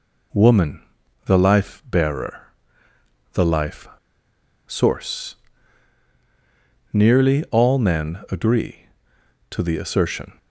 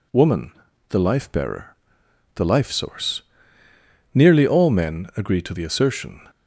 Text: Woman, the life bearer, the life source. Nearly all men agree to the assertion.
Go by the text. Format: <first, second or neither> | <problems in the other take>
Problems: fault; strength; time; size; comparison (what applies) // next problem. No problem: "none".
second | pauses between "life" and "source"; noticeable; at 3.8 s; 0.78 s long